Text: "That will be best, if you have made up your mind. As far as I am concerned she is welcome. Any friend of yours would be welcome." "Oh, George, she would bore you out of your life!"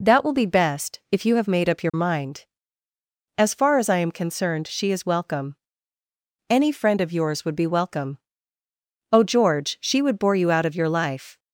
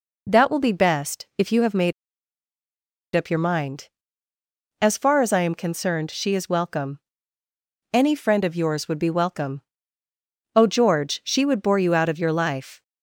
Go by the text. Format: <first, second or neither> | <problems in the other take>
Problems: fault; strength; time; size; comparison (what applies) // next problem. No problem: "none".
first | pauses between "made" and "up"; at 1.9 s; 1.2 s long